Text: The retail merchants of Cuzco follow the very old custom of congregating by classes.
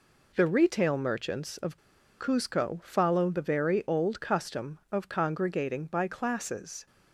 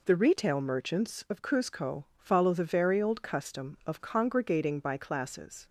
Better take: second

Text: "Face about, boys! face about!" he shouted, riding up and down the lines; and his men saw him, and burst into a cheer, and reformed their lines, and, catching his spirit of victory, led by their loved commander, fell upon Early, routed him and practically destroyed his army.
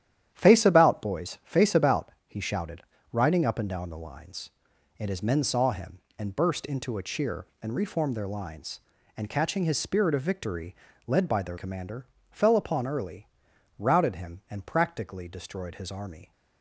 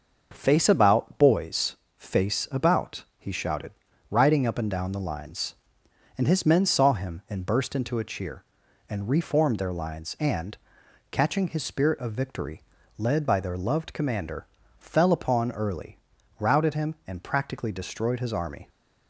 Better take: second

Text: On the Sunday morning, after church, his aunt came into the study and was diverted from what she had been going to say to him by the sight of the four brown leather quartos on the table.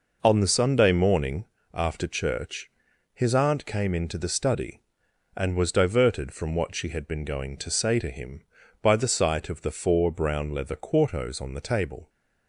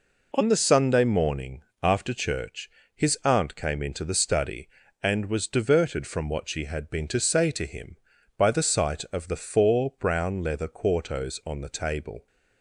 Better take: first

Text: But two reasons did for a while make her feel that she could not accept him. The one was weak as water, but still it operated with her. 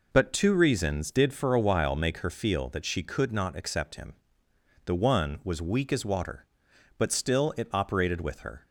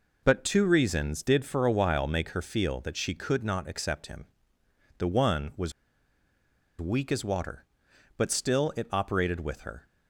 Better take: first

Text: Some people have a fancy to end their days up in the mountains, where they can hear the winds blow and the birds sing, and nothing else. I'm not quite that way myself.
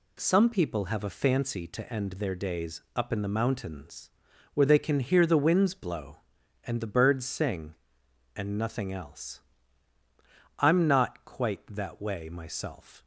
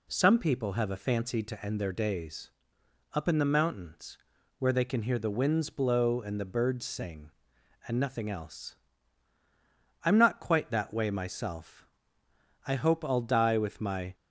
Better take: first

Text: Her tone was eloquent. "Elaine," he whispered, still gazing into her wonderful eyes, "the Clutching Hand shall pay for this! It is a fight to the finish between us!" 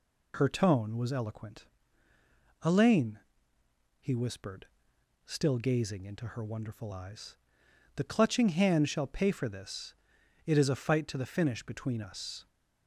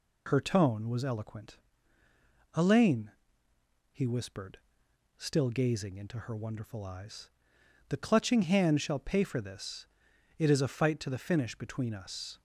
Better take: neither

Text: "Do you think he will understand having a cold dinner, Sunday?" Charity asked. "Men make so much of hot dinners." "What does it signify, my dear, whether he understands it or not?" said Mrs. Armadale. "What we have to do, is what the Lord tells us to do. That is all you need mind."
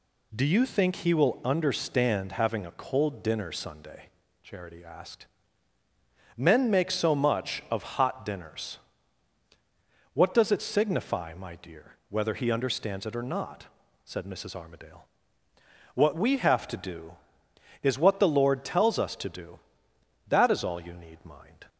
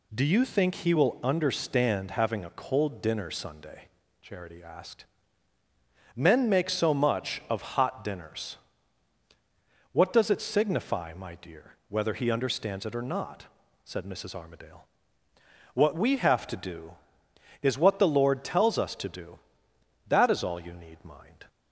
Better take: neither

